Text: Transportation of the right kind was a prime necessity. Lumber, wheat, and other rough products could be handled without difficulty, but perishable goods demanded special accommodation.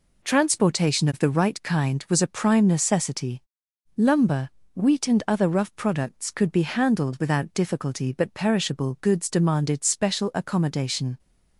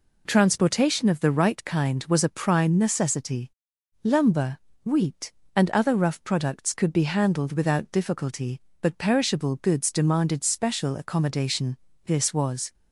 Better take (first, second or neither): first